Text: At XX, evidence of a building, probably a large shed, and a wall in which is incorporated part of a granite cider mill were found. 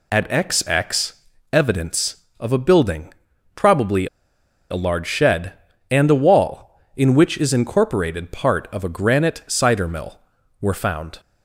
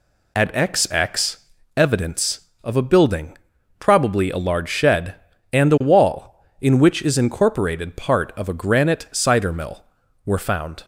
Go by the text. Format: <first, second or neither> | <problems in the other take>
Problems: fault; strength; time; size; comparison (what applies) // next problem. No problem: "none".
second | pauses between "probably" and "a"; noticeable; at 4.0 s; 0.64 s long